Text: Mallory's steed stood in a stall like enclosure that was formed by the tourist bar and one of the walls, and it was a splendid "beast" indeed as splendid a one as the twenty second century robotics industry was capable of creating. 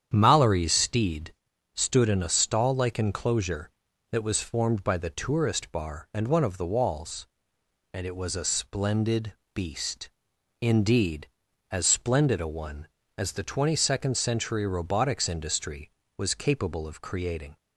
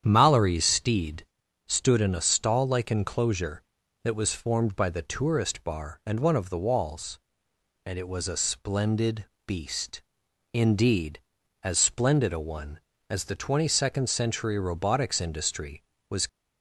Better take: first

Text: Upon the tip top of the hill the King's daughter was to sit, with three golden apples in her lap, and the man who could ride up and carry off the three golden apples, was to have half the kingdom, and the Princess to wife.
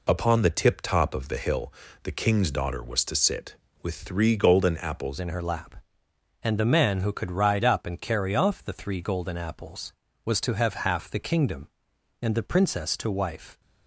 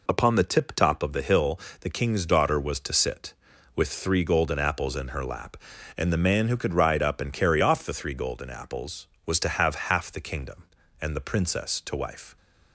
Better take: second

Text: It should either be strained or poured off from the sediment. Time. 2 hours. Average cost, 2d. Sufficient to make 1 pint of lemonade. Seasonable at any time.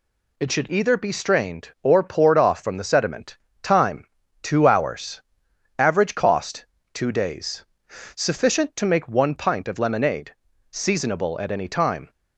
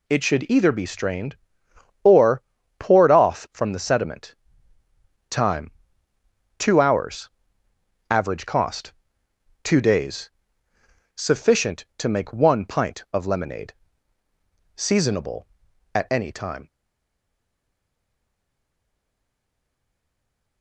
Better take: first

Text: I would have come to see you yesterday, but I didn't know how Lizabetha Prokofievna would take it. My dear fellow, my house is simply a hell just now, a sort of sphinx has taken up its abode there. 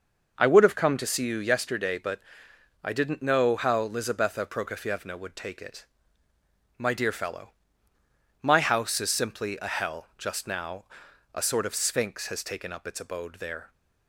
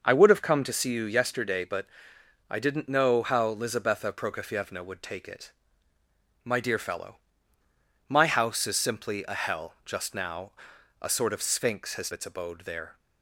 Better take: first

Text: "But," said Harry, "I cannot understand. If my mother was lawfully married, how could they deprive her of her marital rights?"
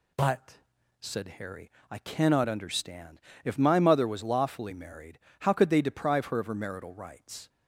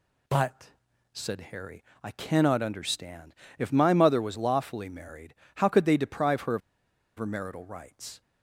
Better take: first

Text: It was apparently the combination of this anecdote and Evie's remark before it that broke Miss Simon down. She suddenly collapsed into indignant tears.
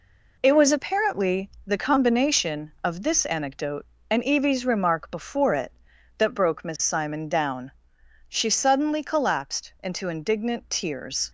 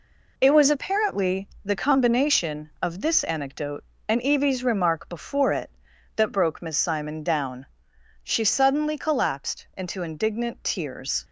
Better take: neither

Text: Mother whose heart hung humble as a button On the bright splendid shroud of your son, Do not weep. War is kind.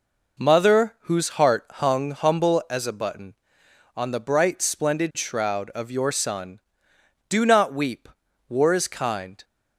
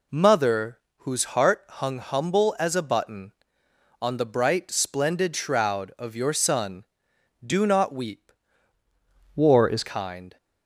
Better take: first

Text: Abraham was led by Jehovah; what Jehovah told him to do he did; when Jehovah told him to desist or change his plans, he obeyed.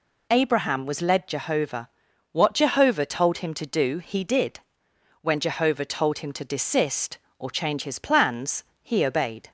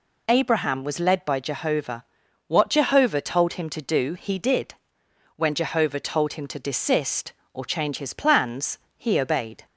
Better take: second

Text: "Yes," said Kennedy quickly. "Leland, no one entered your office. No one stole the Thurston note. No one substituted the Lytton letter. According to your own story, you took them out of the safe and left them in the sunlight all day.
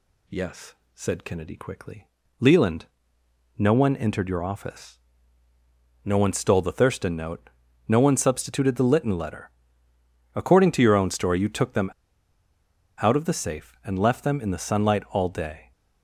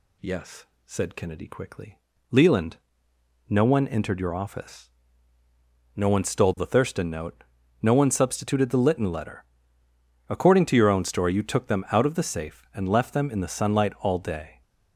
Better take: second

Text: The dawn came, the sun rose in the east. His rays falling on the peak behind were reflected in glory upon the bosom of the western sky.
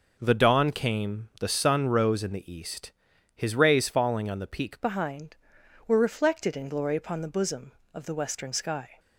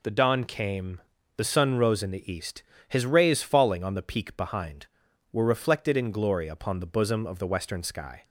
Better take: second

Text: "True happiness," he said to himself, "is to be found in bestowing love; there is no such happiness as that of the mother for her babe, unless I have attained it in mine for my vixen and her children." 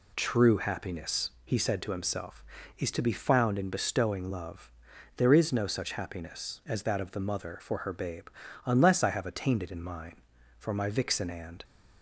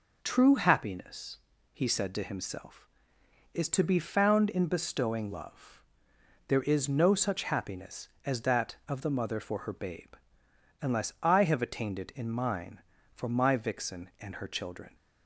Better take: second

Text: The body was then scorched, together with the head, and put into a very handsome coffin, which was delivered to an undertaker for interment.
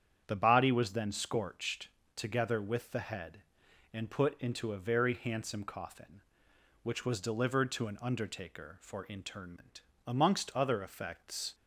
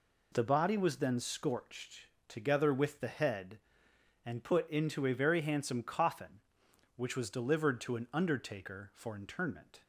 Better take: second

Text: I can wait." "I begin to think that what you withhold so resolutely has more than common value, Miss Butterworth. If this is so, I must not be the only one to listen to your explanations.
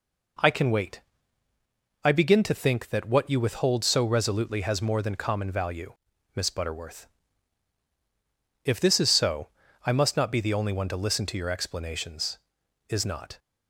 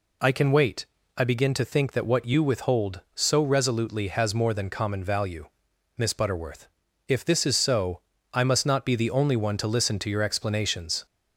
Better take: second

